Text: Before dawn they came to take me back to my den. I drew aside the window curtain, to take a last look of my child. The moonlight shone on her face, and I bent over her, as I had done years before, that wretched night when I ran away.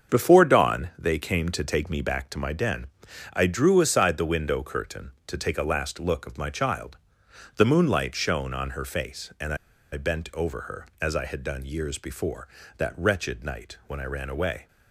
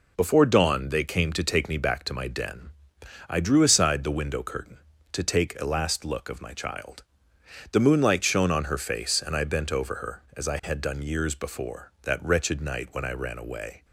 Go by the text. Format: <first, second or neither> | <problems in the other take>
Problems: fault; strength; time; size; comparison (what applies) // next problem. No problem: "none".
second | starts louder than the rest; until 1.1 s; 7 dB // pauses between "and" and "I"; at 9.5 s; 0.38 s long